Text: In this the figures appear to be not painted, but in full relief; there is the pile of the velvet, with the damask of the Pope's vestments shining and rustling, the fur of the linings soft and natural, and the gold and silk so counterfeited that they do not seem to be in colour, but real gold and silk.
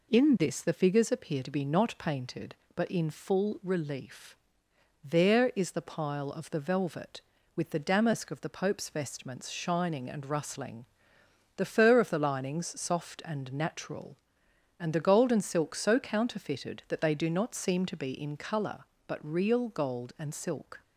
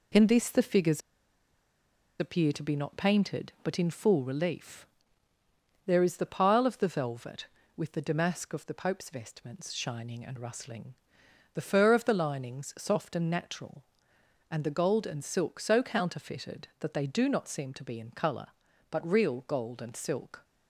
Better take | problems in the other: first | pauses between "figures" and "appear"; at 1.0 s; 1.1 s long

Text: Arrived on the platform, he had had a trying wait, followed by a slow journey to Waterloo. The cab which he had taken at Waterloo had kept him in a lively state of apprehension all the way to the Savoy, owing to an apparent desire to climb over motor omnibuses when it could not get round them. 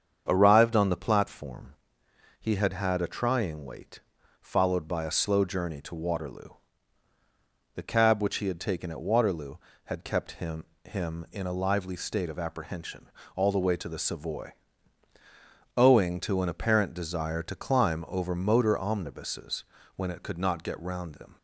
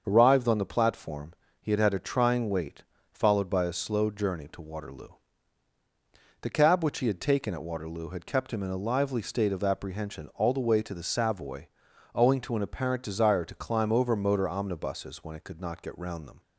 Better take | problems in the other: second | starts louder than the rest; strong; until 1.2 s; 7.5 dB; also in the second // says "him" twice; at 10.8 s // pauses between "apprehension" and "all"; slight; at 13.0 s; 0.28 s long // pauses between "omnibuses" and "when"; slight; at 19.6 s; 0.32 s long

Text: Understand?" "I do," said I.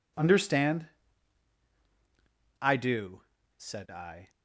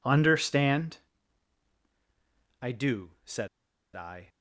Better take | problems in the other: first | pauses between "said" and "I"; noticeable; at 3.4 s; 0.48 s long

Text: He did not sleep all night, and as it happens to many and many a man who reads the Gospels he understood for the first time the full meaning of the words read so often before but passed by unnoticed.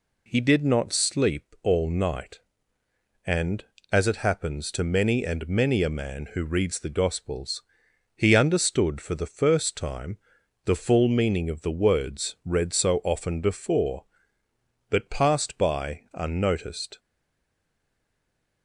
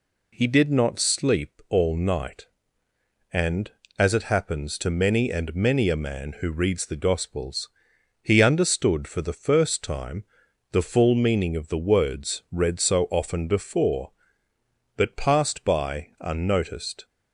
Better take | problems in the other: second | pauses between "Gospels" and "he"; noticeable; at 7.6 s; 0.50 s long; noticeable in the second // pauses between "time" and "the"; noticeable; at 10.1 s; 0.48 s long; noticeable in the second // stays silent after the last word; noticeable; from 16.9 s on; 1.7 s long

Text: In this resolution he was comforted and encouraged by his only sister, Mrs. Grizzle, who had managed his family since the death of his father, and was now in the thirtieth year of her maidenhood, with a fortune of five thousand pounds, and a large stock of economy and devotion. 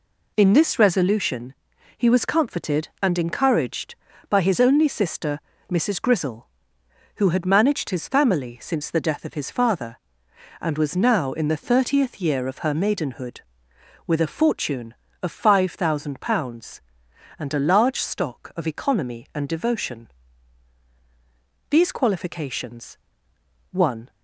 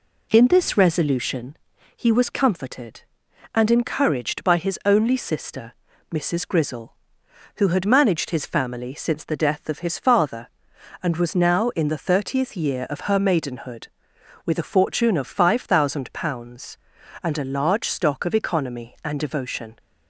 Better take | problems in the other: second | pauses between "resolution" and "he"; at 1.5 s; 0.42 s long; also in the second // goes on to say "These qualifications one"; strong; from 21.7 s on; 2.3 s long

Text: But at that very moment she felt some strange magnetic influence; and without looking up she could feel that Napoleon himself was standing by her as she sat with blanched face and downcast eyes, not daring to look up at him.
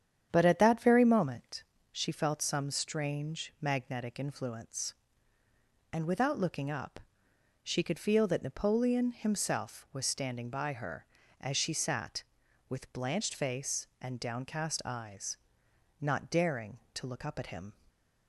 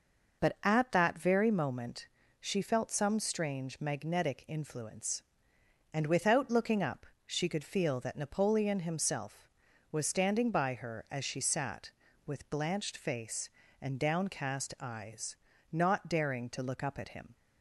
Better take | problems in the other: second | starts louder than the rest; strong; until 1.9 s; 9 dB // pauses between "moment" and "she"; slight; at 1.6 s; 0.28 s long; slight in the second // pauses between "up" and "she"; noticeable; at 6.9 s; 0.64 s long; slight in the second

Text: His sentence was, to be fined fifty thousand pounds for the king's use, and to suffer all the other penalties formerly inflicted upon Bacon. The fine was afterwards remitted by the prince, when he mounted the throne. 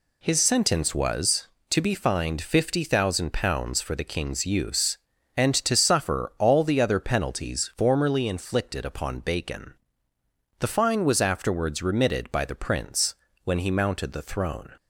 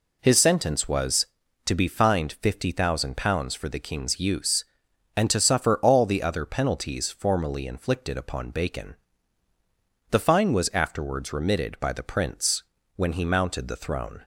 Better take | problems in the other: neither | none

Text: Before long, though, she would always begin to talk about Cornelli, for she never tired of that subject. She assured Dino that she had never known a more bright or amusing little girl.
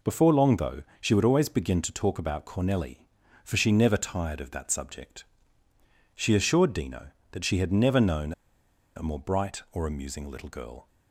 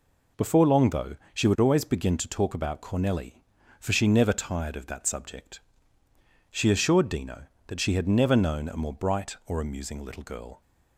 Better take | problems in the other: second | pauses between "known" and "a"; noticeable; at 8.3 s; 0.63 s long

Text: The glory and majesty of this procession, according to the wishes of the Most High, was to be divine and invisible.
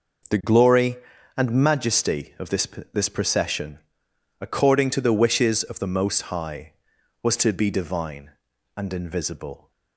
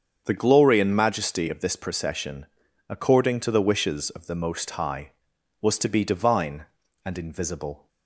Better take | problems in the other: second | starts louder than the rest; until 1.7 s; 6.5 dB; strong in the second // says "this" twice; at 2.9 s

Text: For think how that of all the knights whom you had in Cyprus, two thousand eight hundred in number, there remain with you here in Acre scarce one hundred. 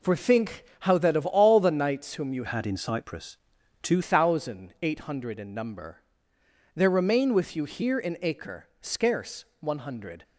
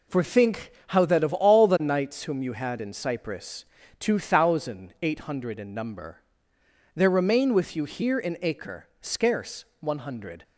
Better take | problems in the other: second | pauses between "think" and "how"; slight; at 0.6 s; 0.16 s long; slight in the second // changes voice from "had" to "two"; from 2.4 to 4.0 s; 1.6 s long // pauses between "scarce" and "one"; slight; at 9.4 s; 0.16 s long; slight in the second

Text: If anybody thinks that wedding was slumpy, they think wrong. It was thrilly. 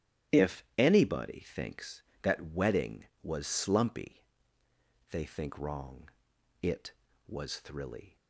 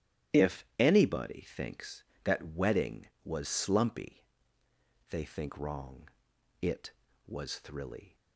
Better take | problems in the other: neither | starts louder than the rest; strong; the same in both

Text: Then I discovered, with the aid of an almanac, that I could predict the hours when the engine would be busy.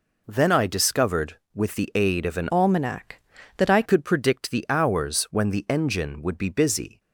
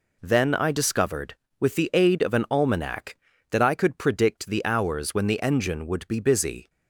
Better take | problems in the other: second | changes voice from "almanac" to "I"; from 2.4 to 3.8 s; 1.4 s long

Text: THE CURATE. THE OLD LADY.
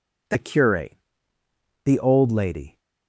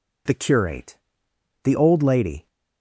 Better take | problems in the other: neither | none

